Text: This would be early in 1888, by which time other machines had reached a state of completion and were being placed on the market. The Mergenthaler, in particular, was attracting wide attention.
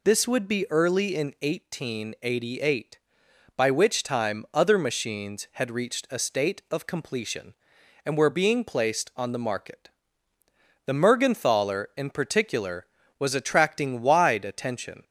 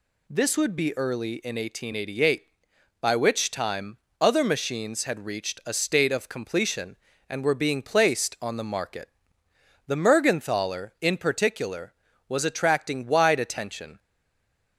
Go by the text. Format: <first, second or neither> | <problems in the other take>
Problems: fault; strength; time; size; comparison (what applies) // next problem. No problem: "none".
first | pauses between "time" and "other"; slight; at 3.9 s; 0.24 s long // stays silent after the last word; slight; from 13.9 s on; 0.8 s long